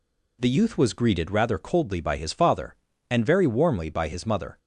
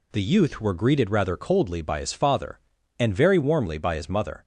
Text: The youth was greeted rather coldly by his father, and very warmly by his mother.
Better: first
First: none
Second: says "were" for "was"; at 0.5 s

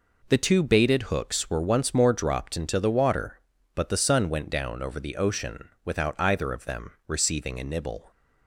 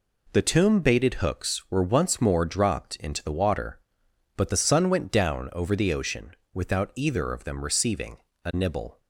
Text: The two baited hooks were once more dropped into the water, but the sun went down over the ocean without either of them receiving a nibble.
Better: first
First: none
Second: says "tomb" for "two"; at 0.4 s // pauses between "ocean" and "without"; slight; at 6.3 s; 0.22 s long // pauses between "receiving" and "a"; slight; at 8.1 s; 0.26 s long

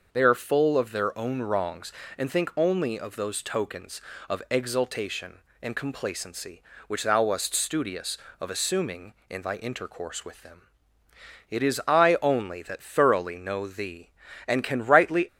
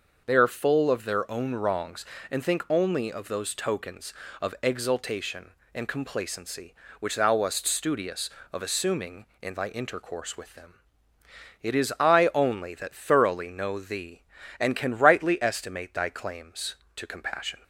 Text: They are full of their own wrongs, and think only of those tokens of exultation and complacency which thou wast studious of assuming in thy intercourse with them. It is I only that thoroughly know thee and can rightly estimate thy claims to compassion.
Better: second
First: starts louder than the rest; noticeable; until 1.1 s; 6 dB // stops before "estimate thy claims to compassion"; at 15.2 s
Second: starts louder than the rest; noticeable; until 1.2 s; 6 dB

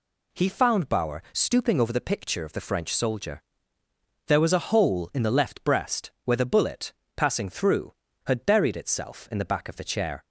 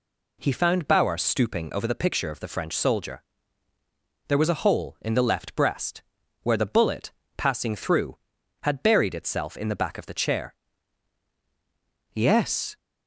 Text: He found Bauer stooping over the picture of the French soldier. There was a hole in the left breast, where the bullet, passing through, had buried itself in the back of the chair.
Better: first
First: none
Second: goes on to say "Yes"; noticeable; from 12.1 s on; 0.64 s long

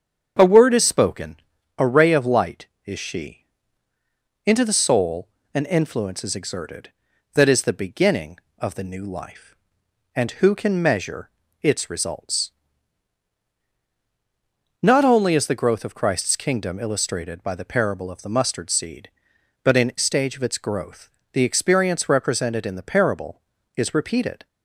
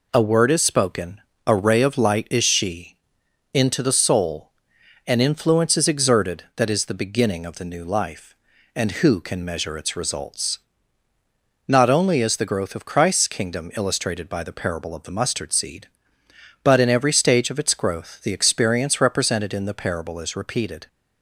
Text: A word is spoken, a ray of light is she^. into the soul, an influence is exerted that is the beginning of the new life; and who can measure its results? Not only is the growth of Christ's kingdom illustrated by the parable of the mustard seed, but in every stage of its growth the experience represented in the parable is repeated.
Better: second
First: starts louder than the rest; strong; until 1.8 s; 7.5 dB // pauses between "measure" and "its"; slight; at 11.3 s; 0.32 s long // skips "every"; at 19.9 s // pauses between "growth" and "the"; slight; at 21.1 s; 0.22 s long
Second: none

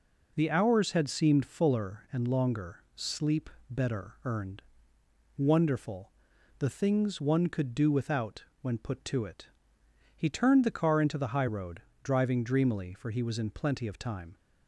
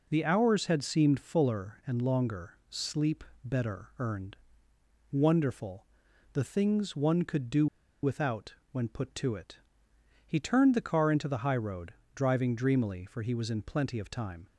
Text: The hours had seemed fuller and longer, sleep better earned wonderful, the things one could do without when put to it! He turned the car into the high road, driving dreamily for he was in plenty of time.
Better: first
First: pauses between "sleep" and "better"; slight; at 3.4 s; 0.20 s long // pauses between "earned" and "wonderful"; noticeable; at 4.6 s; 0.74 s long // pauses between "without" and "when"; slight; at 8.4 s; 0.16 s long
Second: pauses between "sleep" and "better"; slight; at 3.2 s; 0.20 s long // pauses between "earned" and "wonderful"; noticeable; at 4.3 s; 0.74 s long // pauses between "do" and "without"; at 7.6 s; 0.37 s long // pauses between "without" and "when"; slight; at 8.5 s; 0.16 s long

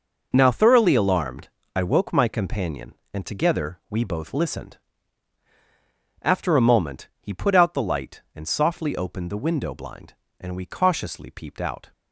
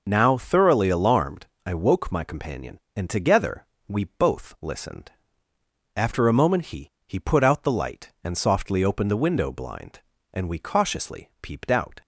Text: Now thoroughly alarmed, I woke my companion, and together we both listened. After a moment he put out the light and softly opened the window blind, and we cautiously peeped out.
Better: first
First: none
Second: pauses between "together" and "we"; slight; at 3.6 s; 0.22 s long // says "he" twice; at 7.0 s

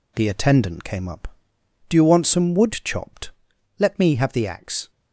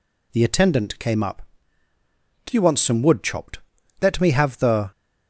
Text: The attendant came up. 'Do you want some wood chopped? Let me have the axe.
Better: first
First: none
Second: stops before "axe"; at 4.9 s

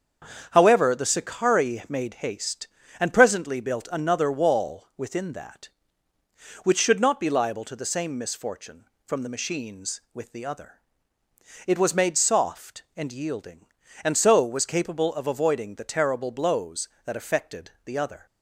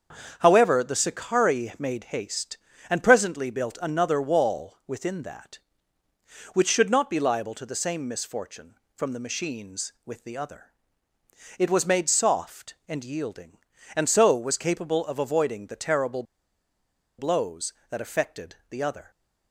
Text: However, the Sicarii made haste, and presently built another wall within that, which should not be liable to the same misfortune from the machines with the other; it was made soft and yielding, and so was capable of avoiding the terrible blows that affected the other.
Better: first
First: starts louder than the rest; strong; until 1.5 s; 7.5 dB // pauses between "affected" and "the"; slight; at 17.6 s; 0.16 s long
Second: starts louder than the rest; strong; until 1.4 s; 7 dB // pauses between "terrible" and "blows"; noticeable; at 16.2 s; 0.95 s long // pauses between "affected" and "the"; slight; at 18.5 s; 0.16 s long

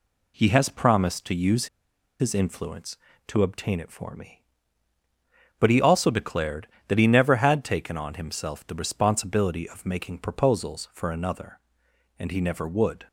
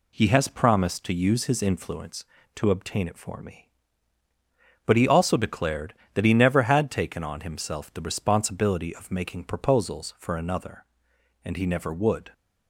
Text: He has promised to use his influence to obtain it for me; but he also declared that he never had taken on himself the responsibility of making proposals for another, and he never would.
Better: second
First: pauses between "use" and "his"; noticeable; at 1.6 s; 0.53 s long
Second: none

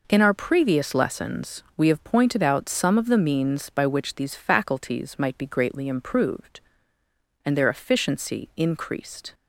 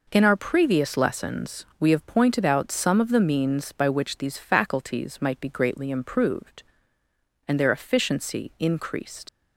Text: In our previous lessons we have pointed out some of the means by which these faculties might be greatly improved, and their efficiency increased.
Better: first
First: none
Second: leaves "increased" unfinished; at 9.2 s; 75 ms

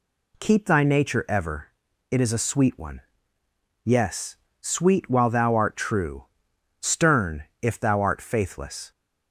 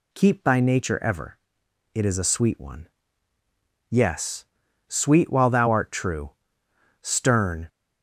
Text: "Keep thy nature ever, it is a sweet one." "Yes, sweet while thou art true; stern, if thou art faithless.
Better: first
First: none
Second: stops before "if thou art faithless"; at 7.6 s

